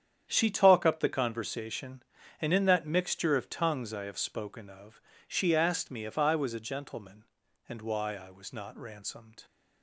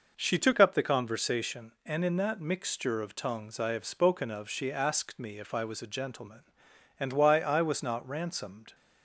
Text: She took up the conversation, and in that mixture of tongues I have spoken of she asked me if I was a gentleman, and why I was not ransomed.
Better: second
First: starts louder than the rest; strong; until 1.2 s; 9 dB // says "talk" for "took"; at 0.5 s // pauses between "of" and "she"; slight; at 5.0 s; 0.28 s long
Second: none

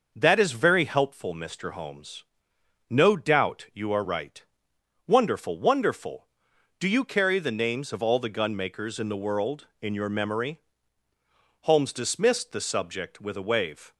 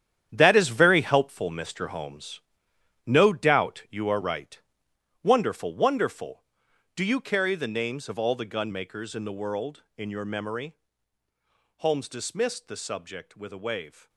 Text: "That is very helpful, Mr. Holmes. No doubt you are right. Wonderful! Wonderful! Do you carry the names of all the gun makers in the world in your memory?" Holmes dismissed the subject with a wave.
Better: first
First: none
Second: gets quieter; strong; throughout; 11 dB

